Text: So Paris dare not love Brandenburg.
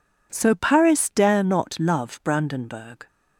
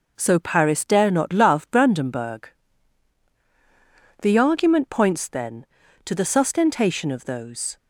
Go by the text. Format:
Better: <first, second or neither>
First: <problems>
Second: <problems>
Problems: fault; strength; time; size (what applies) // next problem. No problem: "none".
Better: first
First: none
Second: goes on to say "The argument points then to the sustentation of those"; strong; from 4.2 s on; 3.5 s long